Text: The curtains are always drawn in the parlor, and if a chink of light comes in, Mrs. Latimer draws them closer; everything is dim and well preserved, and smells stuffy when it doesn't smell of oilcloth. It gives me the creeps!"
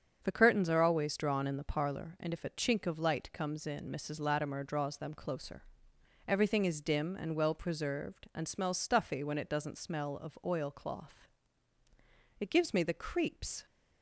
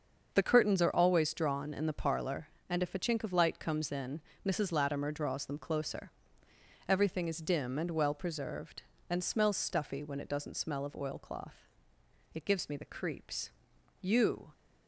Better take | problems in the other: first | starts louder than the rest; until 1.3 s; 6.5 dB; strong in the first // goes on to say "You"; from 13.9 s on; 0.52 s long

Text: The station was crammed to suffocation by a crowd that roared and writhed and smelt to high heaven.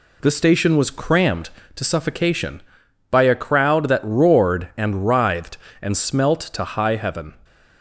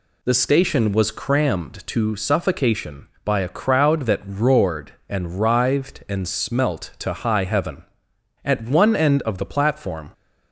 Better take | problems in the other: first | goes on to say "At one end of the platform"; from 8.4 s on; 1.6 s long

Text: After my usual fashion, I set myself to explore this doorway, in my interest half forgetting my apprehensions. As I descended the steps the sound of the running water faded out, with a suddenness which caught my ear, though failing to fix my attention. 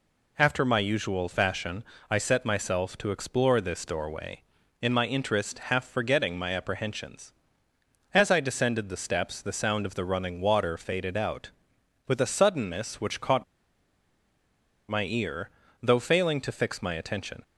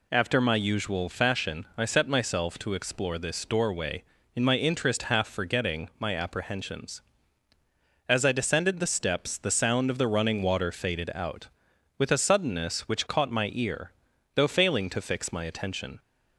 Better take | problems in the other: second | pauses between "caught" and "my"; strong; at 13.4 s; 1.4 s long

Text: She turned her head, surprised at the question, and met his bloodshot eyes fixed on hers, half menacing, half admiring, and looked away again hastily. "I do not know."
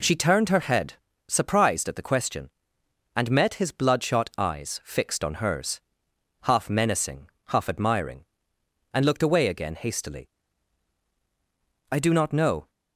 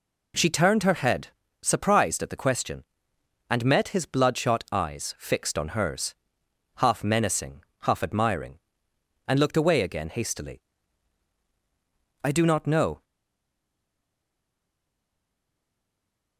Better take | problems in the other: first | stays silent after the last word; strong; from 13.0 s on; 3.3 s long

